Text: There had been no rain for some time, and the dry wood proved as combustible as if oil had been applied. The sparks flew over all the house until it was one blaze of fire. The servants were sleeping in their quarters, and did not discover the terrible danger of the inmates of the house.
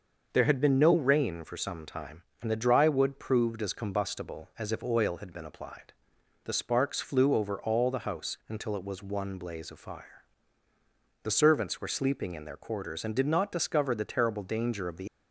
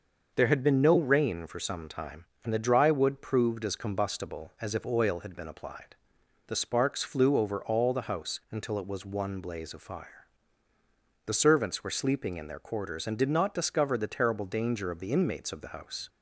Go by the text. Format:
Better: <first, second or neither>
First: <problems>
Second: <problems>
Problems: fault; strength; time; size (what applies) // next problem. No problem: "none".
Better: second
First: starts louder than the rest; until 1.3 s; 6 dB // stops before "inmates of the house"; at 15.0 s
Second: starts louder than the rest; noticeable; until 1.3 s; 6 dB